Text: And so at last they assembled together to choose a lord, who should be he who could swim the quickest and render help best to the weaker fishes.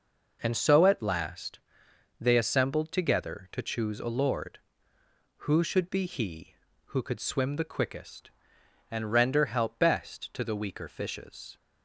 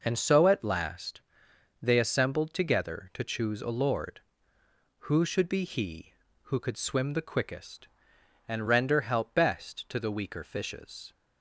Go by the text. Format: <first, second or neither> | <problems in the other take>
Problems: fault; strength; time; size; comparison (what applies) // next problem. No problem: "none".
neither | pauses between "last" and "they"; noticeable; the same in both